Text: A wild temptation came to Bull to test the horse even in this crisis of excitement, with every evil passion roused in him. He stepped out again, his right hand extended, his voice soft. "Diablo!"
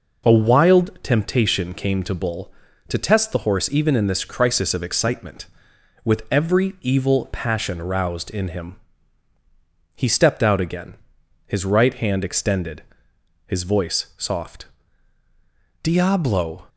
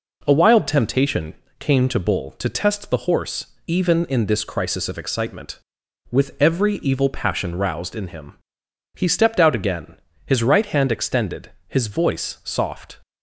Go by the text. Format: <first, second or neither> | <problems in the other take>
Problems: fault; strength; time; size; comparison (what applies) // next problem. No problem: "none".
first | pauses between "temptation" and "came"; slight; at 1.3 s; 0.24 s long // pauses between "horse" and "even"; slight; at 3.4 s; 0.20 s long // stops before "Diablo"; at 13.0 s